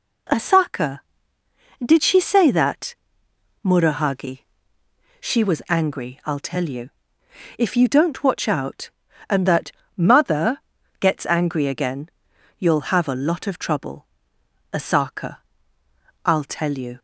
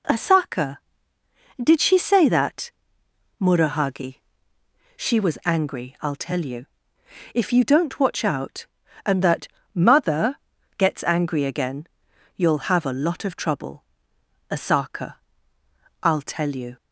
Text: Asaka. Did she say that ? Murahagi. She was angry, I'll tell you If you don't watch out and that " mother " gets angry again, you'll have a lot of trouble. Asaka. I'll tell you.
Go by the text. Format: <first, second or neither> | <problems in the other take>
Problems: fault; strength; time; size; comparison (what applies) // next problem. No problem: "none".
neither | pauses between "you" and "If"; noticeable; the same in both